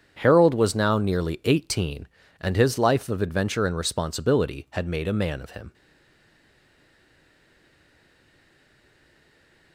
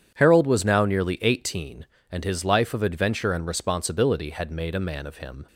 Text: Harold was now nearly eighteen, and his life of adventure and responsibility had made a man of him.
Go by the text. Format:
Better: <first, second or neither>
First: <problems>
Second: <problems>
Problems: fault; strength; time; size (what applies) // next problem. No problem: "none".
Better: second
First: starts louder than the rest; strong; until 1.1 s; 7.5 dB // stays silent after the last word; strong; from 5.7 s on; 4.0 s long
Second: starts louder than the rest; strong; until 1.1 s; 8.5 dB